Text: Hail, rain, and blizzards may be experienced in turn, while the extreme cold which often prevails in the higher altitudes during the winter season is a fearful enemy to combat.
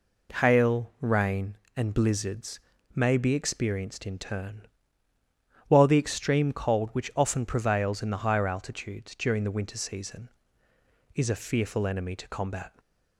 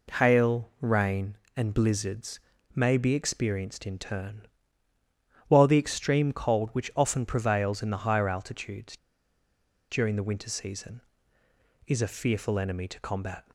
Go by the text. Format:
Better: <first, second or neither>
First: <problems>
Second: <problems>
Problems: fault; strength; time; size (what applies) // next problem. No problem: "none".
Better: first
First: pauses between "blizzards" and "may"; slight; at 2.5 s; 0.36 s long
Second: pauses between "blizzards" and "may"; slight; at 2.3 s; 0.36 s long // pauses between "altitudes" and "during"; noticeable; at 8.9 s; 0.92 s long